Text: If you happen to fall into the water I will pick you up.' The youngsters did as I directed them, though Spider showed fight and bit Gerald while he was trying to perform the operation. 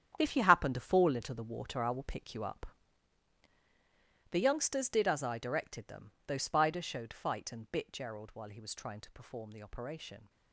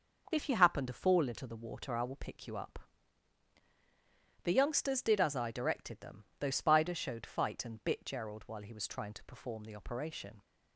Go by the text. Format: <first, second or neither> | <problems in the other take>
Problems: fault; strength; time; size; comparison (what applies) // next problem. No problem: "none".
second | gets quieter; strong; throughout; 12.5 dB